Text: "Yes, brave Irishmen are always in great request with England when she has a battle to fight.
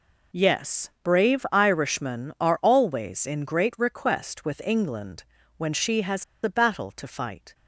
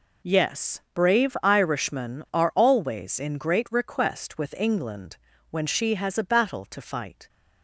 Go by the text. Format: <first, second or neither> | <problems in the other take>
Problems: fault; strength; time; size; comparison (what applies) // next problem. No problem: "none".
second | pauses between "England" and "when"; slight; at 5.2 s; 0.32 s long; slight in the second // pauses between "has" and "a"; slight; at 6.2 s; 0.20 s long